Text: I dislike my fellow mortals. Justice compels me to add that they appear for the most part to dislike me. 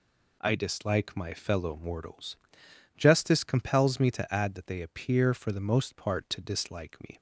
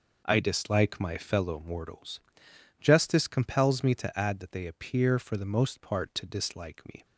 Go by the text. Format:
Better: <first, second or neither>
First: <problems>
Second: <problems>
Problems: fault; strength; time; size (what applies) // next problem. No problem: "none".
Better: first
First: none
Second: starts louder than the rest; noticeable; until 1.4 s; 5.5 dB